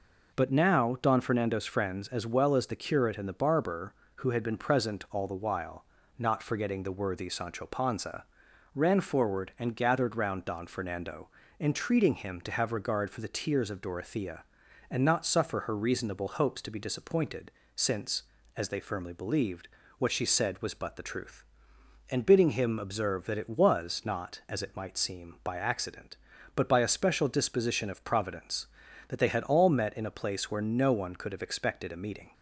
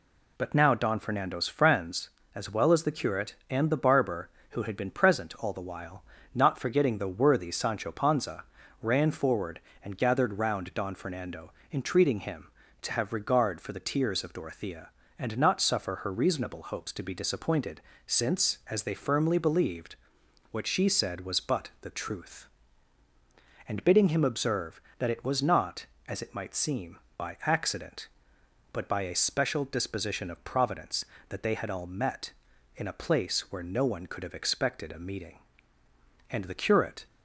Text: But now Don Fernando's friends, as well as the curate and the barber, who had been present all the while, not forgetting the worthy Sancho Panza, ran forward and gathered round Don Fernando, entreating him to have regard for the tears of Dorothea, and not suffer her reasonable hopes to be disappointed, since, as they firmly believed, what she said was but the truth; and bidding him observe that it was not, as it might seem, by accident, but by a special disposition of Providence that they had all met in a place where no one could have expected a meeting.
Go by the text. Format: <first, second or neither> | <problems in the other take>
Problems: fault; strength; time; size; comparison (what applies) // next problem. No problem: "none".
first | goes on to say "And the curate"; noticeable; from 36.2 s on; 0.76 s long